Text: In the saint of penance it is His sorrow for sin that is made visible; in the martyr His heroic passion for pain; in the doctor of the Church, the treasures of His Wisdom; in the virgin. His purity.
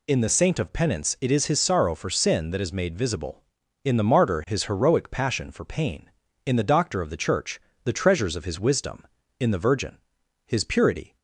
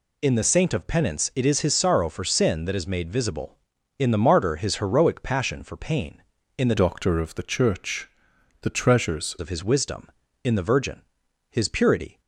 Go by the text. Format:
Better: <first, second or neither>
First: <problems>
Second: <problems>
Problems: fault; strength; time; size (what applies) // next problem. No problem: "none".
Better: first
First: none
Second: changes voice from "doctor" to "treasures"; from 6.7 to 9.3 s; 2.6 s long